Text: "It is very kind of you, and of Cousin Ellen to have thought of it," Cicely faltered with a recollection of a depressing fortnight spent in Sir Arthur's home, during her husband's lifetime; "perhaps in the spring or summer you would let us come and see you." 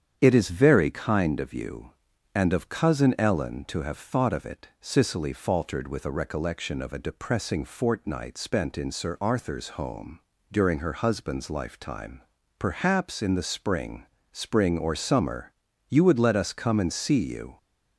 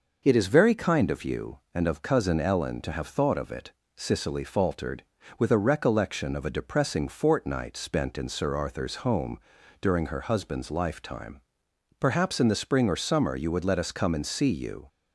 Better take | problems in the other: second | starts louder than the rest; strong; until 1.2 s; 8.5 dB // says "spring" twice; at 14.3 s // pauses between "summer" and "you"; at 15.5 s; 0.38 s long

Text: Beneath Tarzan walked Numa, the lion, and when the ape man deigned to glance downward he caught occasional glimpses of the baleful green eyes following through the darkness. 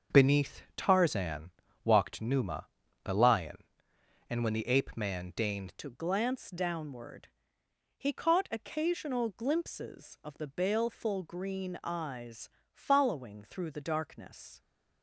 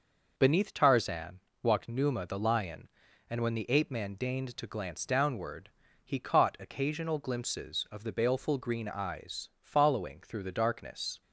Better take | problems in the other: second | starts louder than the rest; until 1.2 s; 6.5 dB // pauses between "Tarzan" and "walked"; slight; at 1.5 s; 0.34 s long; slight in the second // changes voice at "to"; from 5.7 s on; 8.9 s long // pauses between "downward" and "he"; noticeable; at 7.2 s; 0.70 s long; slight in the second // pauses between "eyes" and "following"; slight; at 12.5 s; 0.24 s long

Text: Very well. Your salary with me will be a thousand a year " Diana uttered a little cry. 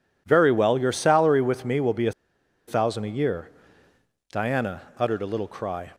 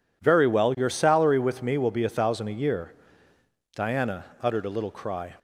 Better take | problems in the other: second | pauses between "a" and "thousand"; noticeable; at 2.1 s; 0.55 s long // pauses between "Diana" and "uttered"; slight; at 4.8 s; 0.16 s long; slight in the second

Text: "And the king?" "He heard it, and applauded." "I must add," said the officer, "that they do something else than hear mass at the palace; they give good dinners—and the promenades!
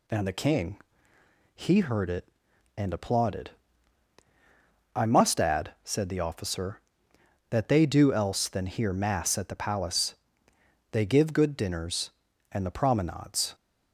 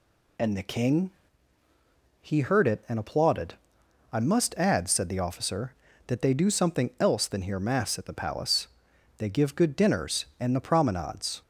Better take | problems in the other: second | skips "something"; at 8.1 s

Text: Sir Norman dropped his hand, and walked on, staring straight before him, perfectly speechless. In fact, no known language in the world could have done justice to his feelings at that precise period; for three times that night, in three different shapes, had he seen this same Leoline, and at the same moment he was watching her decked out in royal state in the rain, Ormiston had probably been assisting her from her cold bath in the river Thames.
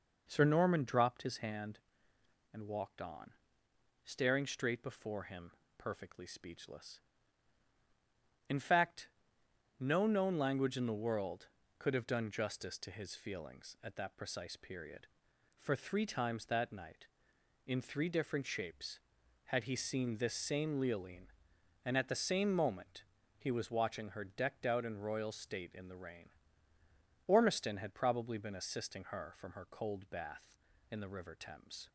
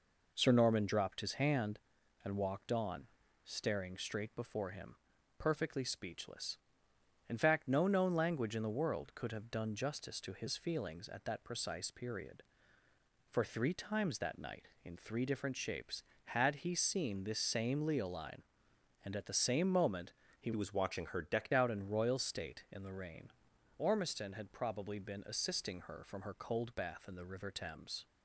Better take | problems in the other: first | pauses between "moment" and "he"; slight; at 20.1 s; 0.26 s long; slight in the first // changes voice from "was" to "decked"; from 20.5 to 21.5 s; 1.0 s long

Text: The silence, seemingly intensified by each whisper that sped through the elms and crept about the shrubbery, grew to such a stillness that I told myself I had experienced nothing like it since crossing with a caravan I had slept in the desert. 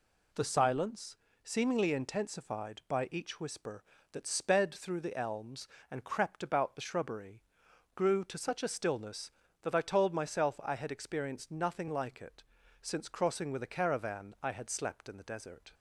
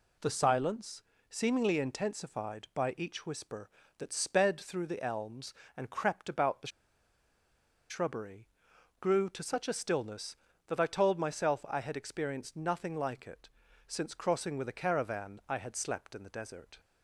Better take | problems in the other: first | pauses between "the" and "shrubbery"; at 6.6 s; 1.2 s long // pauses between "it" and "since"; at 13.4 s; 0.38 s long; also in the first

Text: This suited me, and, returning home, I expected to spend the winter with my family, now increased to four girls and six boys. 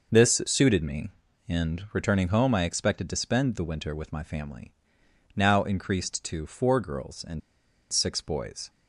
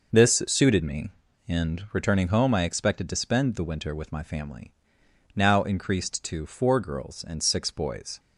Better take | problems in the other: second | pauses between "and" and "six"; noticeable; at 7.4 s; 0.53 s long

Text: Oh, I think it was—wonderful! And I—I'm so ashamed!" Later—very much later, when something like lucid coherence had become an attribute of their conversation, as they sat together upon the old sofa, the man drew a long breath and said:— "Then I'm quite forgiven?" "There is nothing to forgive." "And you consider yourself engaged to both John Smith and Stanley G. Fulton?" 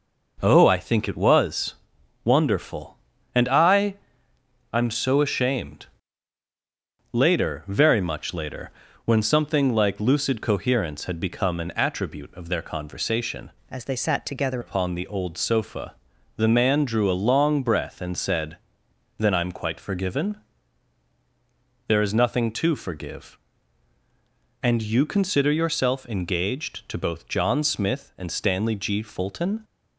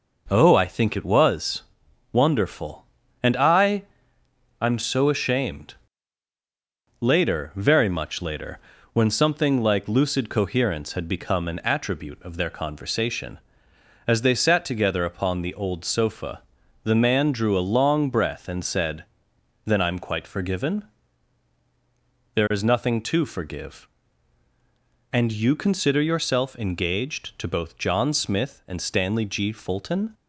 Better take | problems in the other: second | changes voice from "as" to "together"; from 13.7 to 14.6 s; 0.9 s long

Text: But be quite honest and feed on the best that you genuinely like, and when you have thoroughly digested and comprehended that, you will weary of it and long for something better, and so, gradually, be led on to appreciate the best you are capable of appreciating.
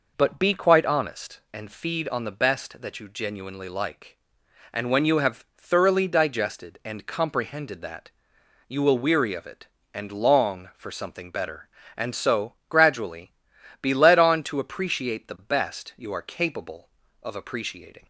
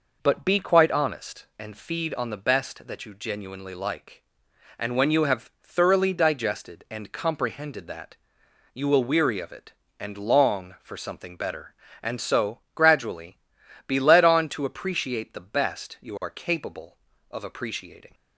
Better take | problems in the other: neither | none

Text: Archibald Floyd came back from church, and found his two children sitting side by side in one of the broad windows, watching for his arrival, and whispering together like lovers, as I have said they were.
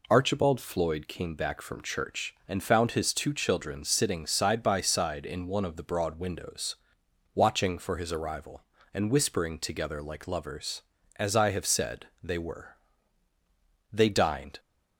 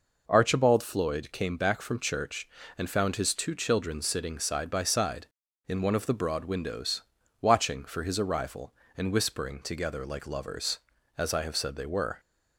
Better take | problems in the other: second | pauses between "said" and "they"; slight; at 12.0 s; 0.16 s long // goes on to say "They dined"; noticeable; from 13.9 s on; 0.68 s long

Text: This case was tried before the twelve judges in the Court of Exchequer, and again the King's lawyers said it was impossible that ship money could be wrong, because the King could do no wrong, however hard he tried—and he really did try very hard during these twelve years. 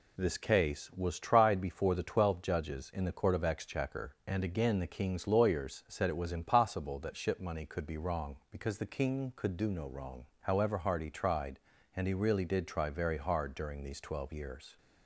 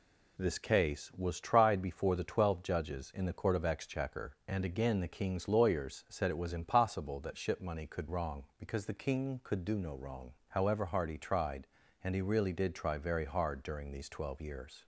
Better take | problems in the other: first | skips "be"; at 8.0 s

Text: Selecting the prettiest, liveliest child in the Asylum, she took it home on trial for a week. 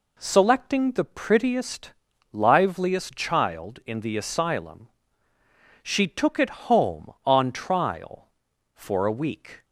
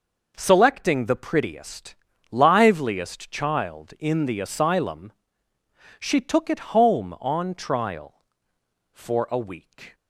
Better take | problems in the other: neither | none

